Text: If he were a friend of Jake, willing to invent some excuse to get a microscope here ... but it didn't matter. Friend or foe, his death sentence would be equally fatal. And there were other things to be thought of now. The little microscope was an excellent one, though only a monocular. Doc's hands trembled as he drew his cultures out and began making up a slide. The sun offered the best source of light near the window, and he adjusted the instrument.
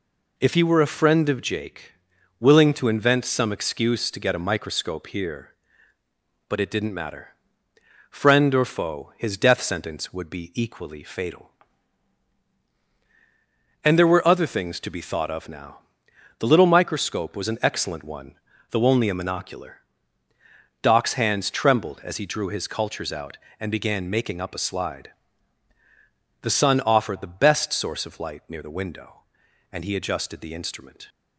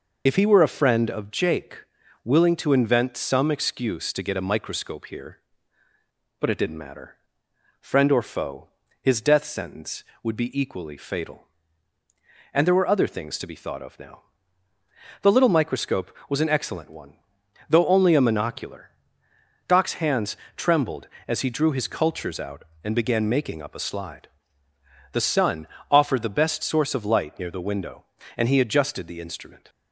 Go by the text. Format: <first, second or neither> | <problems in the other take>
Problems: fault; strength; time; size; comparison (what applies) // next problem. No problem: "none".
first | loses the start of "If"; at 0.2 s; 45 ms // pauses between "hands" and "trembled"; slight; at 20.3 s; 0.22 s long // pauses between "sun" and "offered"; slight; at 25.6 s; 0.24 s long